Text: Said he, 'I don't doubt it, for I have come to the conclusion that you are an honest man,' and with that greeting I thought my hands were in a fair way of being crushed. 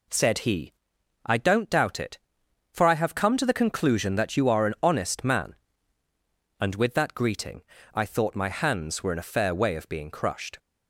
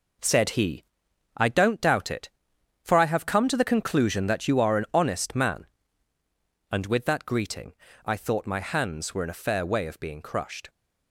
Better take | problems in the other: first | gets quieter; strong; throughout; 8 dB // pauses between "greeting" and "I"; slight; at 7.7 s; 0.32 s long; slight in the first

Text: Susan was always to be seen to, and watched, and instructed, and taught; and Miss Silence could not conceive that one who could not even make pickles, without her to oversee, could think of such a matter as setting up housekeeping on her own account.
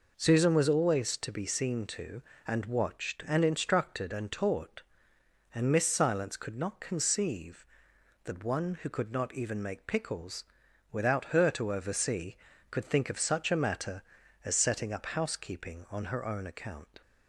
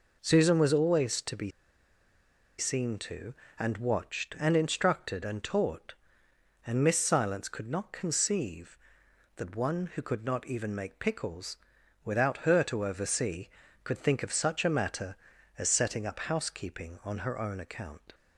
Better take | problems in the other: first | pauses between "be" and "seen"; at 1.4 s; 1.0 s long

